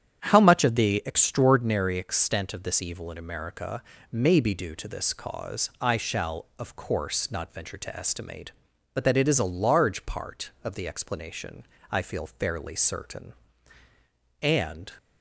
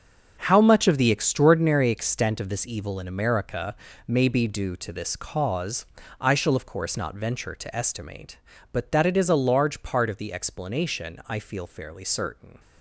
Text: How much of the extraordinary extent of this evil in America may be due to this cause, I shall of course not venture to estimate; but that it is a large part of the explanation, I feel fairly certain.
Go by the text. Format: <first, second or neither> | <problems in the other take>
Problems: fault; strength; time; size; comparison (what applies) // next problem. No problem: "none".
second | starts louder than the rest; strong; until 1.2 s; 9 dB; also in the second // pauses between "America" and "may"; slight; at 3.8 s; 0.30 s long; slight in the second // goes on to say "And"; from 14.4 s on; 0.50 s long